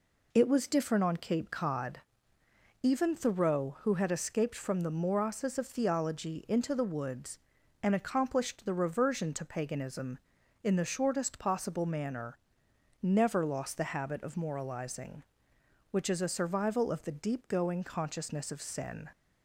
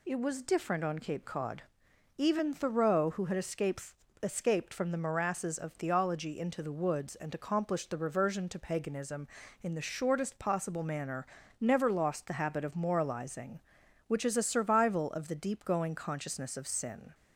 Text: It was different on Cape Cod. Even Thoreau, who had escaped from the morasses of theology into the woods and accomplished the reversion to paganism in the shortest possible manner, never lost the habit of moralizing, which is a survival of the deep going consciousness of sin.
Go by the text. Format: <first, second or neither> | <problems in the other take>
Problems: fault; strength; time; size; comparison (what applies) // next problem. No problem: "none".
first | says "escaped" twice; at 4.2 s